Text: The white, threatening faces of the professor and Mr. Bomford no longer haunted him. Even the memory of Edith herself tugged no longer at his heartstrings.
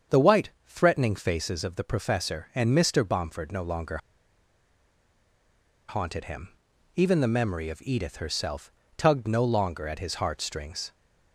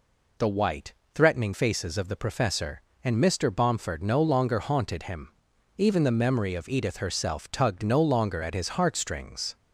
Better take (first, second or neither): second